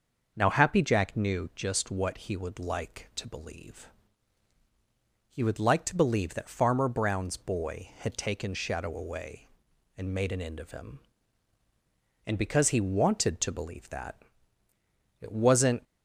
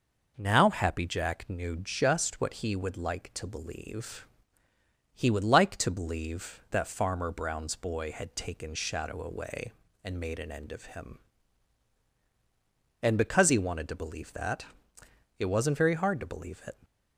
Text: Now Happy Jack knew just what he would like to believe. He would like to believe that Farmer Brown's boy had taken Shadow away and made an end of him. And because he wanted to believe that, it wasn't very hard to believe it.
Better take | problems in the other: second | starts louder than the rest; until 1.3 s; 6.5 dB // stops before "very hard to believe it"; at 15.8 s

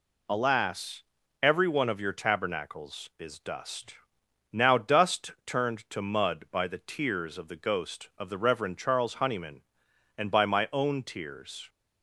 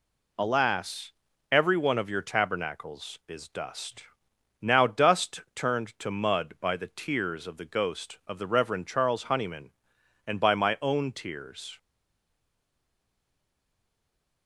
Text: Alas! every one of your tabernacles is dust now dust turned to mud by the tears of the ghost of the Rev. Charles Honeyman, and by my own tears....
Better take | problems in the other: first | pauses between "dust" and "now"; noticeable; at 4.0 s; 0.58 s long; noticeable in the first // stays silent after the last word; strong; from 11.7 s on; 2.7 s long

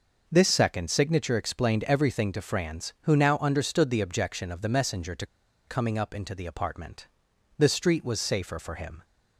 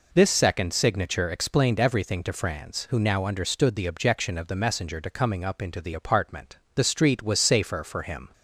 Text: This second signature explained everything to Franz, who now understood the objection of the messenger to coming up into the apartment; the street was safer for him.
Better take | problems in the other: second | pauses between "to" and "coming"; at 5.2 s; 0.42 s long

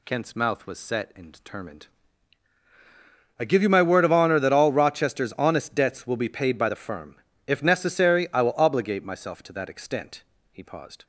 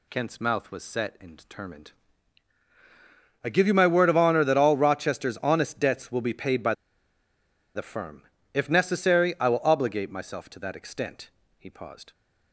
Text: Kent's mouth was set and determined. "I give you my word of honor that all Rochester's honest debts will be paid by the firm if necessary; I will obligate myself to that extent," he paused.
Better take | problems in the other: first | pauses between "by" and "the"; at 6.7 s; 1.0 s long // pauses between "firm" and "if"; slight; at 8.2 s; 0.30 s long; slight in the first

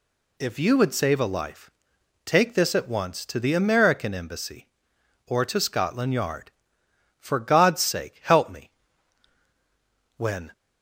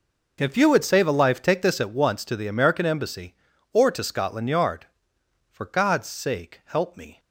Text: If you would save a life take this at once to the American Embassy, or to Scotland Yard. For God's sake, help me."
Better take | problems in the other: second | pauses between "life" and "take"; noticeable; at 1.7 s; 0.54 s long // goes on to say "When"; slight; from 10.1 s on; 0.34 s long

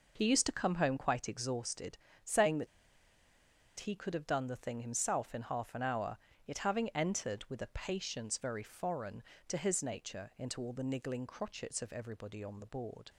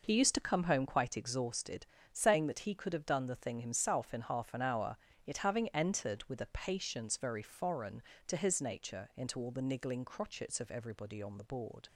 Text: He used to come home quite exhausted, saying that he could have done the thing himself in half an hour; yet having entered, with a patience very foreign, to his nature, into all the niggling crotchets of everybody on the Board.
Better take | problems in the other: second | pauses between "that" and "he"; at 2.6 s; 1.1 s long

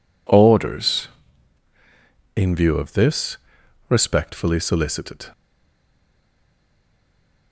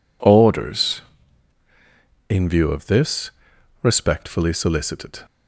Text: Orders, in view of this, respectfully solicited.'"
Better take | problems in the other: second | stays silent after the last word; from 5.3 s on; 2.2 s long

